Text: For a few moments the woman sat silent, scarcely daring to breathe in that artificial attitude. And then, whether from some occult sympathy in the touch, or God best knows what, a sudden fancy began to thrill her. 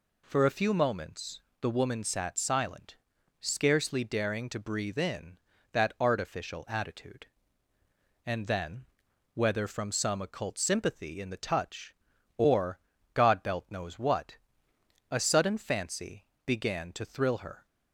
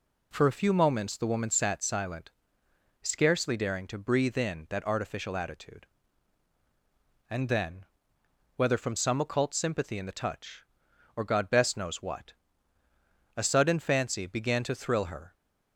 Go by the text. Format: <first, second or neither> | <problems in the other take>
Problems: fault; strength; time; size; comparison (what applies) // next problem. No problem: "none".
second | pauses between "moments" and "the"; slight; at 1.3 s; 0.22 s long // pauses between "or" and "God"; slight; at 12.7 s; 0.34 s long // says "belt" for "best"; at 13.4 s // pauses between "fancy" and "began"; slight; at 16.2 s; 0.20 s long